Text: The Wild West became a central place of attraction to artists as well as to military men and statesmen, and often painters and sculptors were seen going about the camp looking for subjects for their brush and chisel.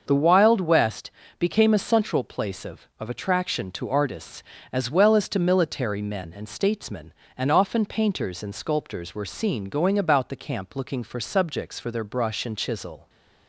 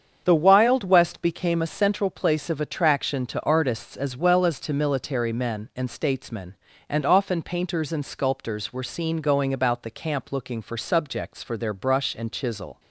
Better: second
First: starts louder than the rest; until 1.0 s; 6.5 dB // pauses between "West" and "became"; slight; at 1.1 s; 0.30 s long // says "of" twice; at 3.0 s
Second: starts louder than the rest; strong; until 1.2 s; 7.5 dB

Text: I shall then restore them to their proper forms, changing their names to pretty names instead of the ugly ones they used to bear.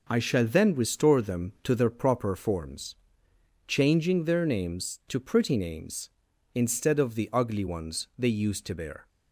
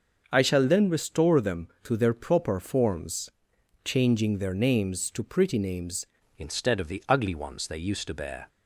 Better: first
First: none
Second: starts louder than the rest; until 1.3 s; 6.5 dB // changes voice at "instead"; from 6.3 s on; 2.1 s long

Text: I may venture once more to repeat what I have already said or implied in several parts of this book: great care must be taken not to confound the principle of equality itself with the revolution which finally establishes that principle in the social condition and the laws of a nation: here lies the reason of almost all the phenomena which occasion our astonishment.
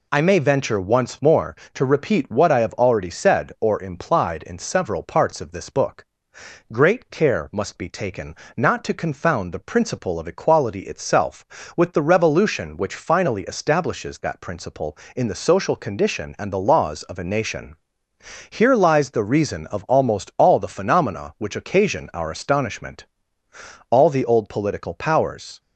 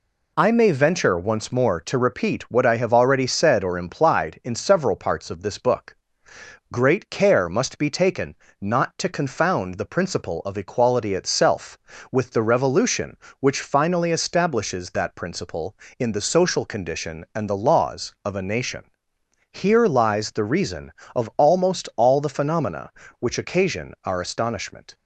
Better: second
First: pauses between "taken" and "not"; slight; at 8.3 s; 0.22 s long // goes on to say "All the old political powers"; strong; from 23.8 s on; 1.7 s long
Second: pauses between "taken" and "not"; slight; at 8.3 s; 0.24 s long

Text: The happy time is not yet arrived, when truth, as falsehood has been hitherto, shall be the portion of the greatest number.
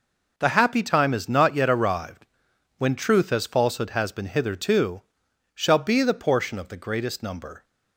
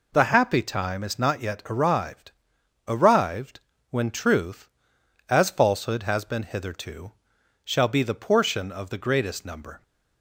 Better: first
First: none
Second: says "arrived" twice; at 2.9 s

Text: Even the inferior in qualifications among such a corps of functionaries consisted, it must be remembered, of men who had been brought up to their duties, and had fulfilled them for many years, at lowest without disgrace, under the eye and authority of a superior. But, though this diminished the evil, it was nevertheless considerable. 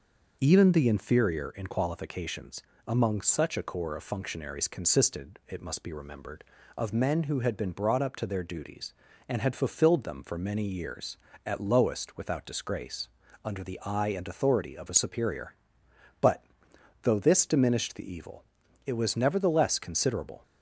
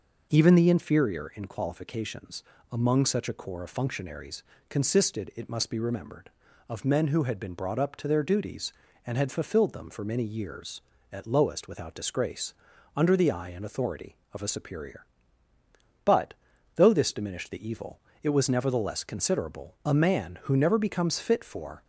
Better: first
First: pauses between "qualifications" and "among"; slight; at 2.6 s; 0.28 s long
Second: pauses between "qualifications" and "among"; slight; at 2.4 s; 0.30 s long // pauses between "functionaries" and "consisted"; slight; at 4.4 s; 0.28 s long // goes on to say "A man who never becomes fit for"; strong; from 19.8 s on; 1.9 s long

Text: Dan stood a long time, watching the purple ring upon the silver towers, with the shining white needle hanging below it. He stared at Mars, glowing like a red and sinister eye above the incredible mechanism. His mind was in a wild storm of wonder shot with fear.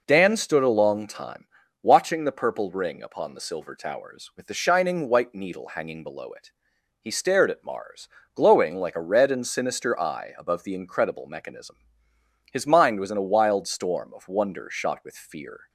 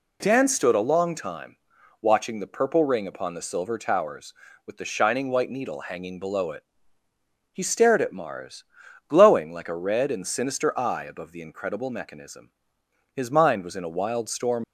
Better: first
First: none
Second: stops before "of wonder shot with fear"; at 14.6 s

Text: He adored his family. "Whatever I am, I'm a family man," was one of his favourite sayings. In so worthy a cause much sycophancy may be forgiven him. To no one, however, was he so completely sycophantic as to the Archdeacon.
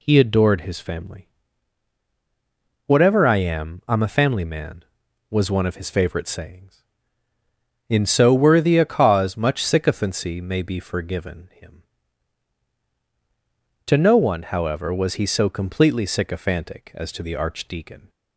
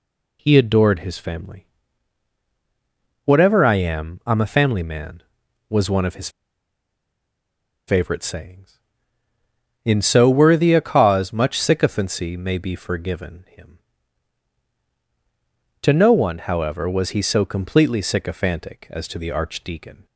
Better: first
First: none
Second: pauses between "his" and "favourite"; strong; at 6.2 s; 1.5 s long

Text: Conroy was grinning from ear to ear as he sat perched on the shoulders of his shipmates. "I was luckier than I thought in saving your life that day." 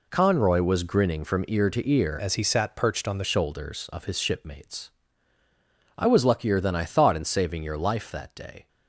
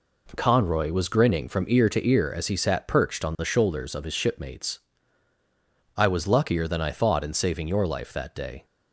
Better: second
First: changes voice from "as" to "the"; from 2.1 to 3.2 s; 1.1 s long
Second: none

